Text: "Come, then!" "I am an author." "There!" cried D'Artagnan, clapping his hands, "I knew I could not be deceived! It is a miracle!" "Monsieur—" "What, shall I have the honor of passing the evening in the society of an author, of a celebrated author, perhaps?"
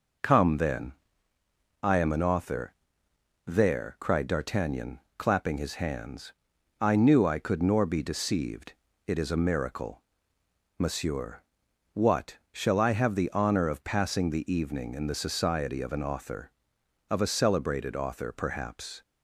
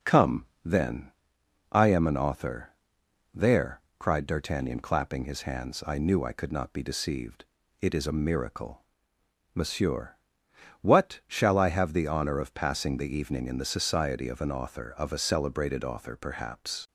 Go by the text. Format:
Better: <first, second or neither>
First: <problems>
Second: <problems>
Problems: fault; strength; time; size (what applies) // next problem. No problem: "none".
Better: second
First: says "nor" for "not"; at 7.6 s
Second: none